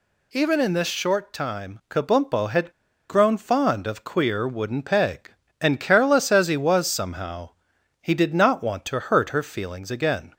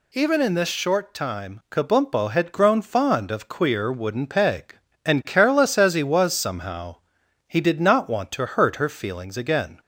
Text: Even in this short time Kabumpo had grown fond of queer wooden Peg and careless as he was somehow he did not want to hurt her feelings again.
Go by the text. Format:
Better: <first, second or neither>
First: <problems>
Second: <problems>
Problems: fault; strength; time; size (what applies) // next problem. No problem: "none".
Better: second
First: pauses between "had" and "grown"; at 2.7 s; 0.38 s long // pauses between "somehow" and "he"; noticeable; at 7.4 s; 0.50 s long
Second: pauses between "somehow" and "he"; noticeable; at 6.9 s; 0.50 s long